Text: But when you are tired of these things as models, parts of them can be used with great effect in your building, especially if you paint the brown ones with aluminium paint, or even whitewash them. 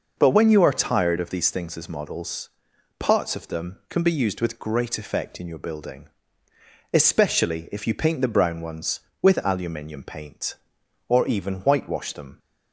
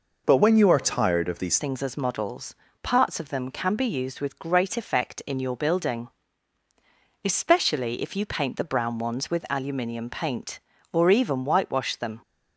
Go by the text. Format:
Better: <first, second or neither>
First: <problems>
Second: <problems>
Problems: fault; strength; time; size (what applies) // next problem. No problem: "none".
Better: first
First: none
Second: changes voice at "things"; from 1.5 s on; 10.7 s long